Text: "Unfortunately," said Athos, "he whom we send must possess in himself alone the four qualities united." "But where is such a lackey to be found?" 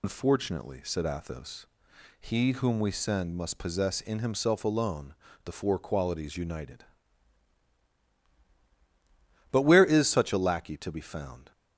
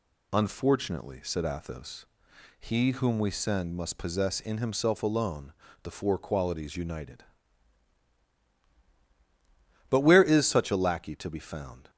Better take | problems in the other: second | loses the start of "Unfortunately"; at 0.0 s; 115 ms // pauses between "alone" and "the"; slight; at 5.1 s; 0.30 s long; slight in the second

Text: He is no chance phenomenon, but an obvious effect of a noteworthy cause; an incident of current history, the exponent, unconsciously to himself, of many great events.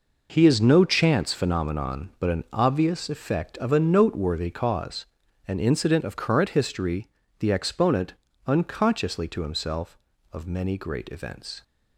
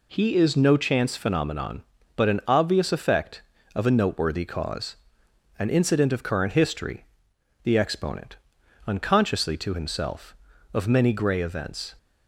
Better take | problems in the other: first | says "grey" for "great"; at 11.1 s

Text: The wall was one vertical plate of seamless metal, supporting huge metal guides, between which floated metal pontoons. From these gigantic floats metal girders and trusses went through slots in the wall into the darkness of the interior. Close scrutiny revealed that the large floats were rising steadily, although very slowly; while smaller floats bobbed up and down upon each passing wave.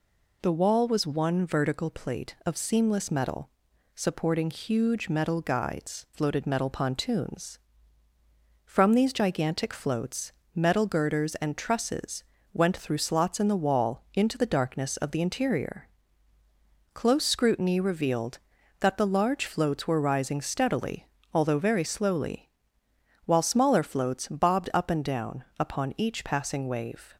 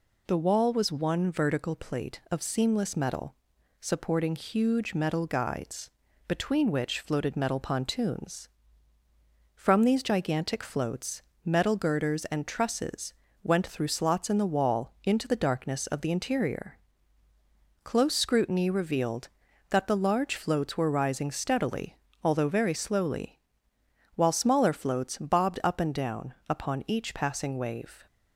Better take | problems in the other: second | skips "between which"; at 6.0 s // pauses between "floats" and "metal"; slight; at 10.3 s; 0.22 s long; slight in the second // pauses between "trusses" and "went"; slight; at 12.2 s; 0.28 s long; slight in the second // pauses between "down" and "upon"; slight; at 25.4 s; 0.16 s long; slight in the second

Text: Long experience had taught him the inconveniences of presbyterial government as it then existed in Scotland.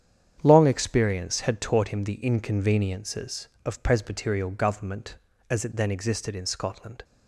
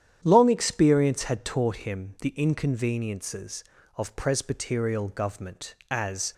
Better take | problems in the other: first | starts louder than the rest; strong; until 1.2 s; 9.5 dB; strong in the first // stops before "it then existed in Scotland"; at 6.3 s

